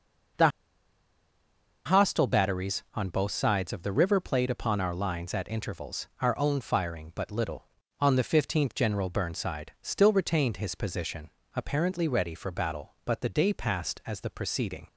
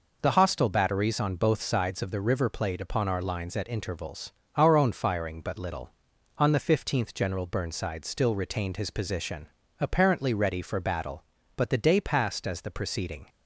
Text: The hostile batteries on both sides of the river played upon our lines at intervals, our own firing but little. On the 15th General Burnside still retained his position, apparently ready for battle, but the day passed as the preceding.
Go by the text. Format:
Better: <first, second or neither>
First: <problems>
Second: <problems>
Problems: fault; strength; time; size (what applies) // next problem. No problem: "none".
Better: second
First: pauses between "The" and "hostile"; strong; at 0.4 s; 1.3 s long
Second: none